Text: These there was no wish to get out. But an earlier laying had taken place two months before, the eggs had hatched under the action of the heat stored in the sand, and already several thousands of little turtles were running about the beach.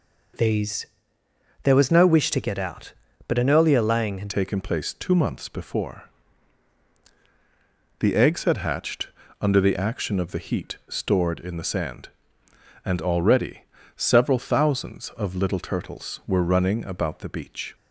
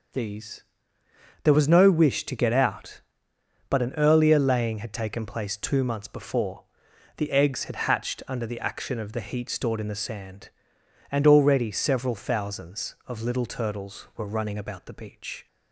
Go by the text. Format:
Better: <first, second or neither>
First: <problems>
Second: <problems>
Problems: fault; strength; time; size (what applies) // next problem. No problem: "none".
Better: second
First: pauses between "These" and "there"; noticeable; at 0.8 s; 0.76 s long // changes voice at "taken"; from 4.2 s on; 13.5 s long // pauses between "hatched" and "under"; slight; at 9.0 s; 0.34 s long // pauses between "already" and "several"; slight; at 13.6 s; 0.32 s long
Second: pauses between "These" and "there"; noticeable; at 0.6 s; 0.80 s long